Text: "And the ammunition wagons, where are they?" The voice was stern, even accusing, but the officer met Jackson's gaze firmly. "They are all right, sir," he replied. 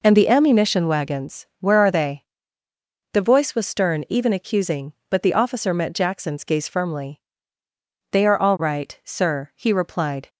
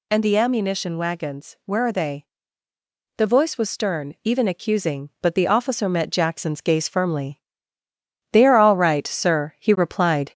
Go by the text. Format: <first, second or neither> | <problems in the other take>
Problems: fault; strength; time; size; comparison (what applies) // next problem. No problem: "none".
first | gets louder; slight; throughout; 2.5 dB